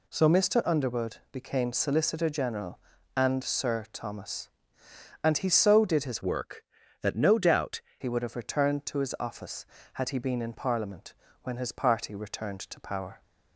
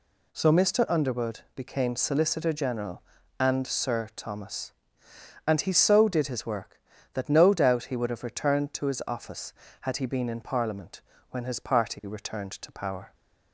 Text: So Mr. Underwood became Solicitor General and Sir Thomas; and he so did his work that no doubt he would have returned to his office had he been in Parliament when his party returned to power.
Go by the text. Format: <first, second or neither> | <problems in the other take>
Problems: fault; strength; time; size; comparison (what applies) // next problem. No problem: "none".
second | pauses between "Underwood" and "became"; slight; at 1.1 s; 0.16 s long; slight in the second // changes voice from "work" to "doubt"; from 6.2 to 7.8 s; 1.6 s long // pauses between "Parliament" and "when"; slight; at 11.1 s; 0.30 s long; slight in the second